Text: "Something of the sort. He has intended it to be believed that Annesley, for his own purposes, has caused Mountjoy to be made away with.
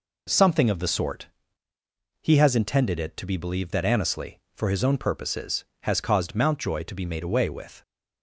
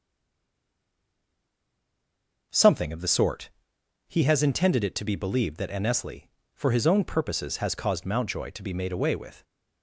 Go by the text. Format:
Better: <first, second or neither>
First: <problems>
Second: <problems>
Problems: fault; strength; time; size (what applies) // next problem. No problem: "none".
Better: first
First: none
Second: stays silent before the first word; until 2.5 s; 2.5 s long